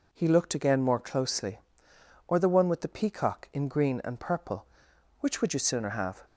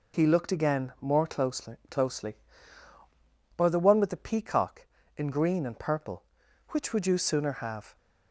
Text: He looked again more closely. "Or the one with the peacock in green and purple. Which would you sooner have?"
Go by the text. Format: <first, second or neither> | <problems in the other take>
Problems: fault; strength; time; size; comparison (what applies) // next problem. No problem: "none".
first | says "closely" twice; at 1.8 s